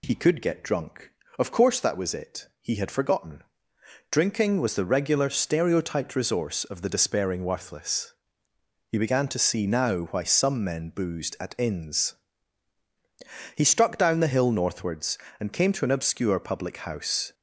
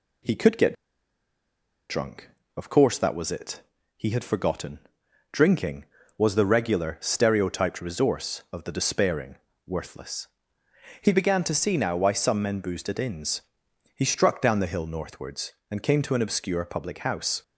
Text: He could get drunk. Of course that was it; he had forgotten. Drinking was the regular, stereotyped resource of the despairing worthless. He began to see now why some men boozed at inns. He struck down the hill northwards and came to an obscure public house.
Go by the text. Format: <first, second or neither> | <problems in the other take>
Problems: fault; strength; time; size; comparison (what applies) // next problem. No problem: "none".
first | pauses between "get" and "drunk"; at 0.7 s; 1.1 s long // pauses between "despairing" and "worthless"; slight; at 9.3 s; 0.28 s long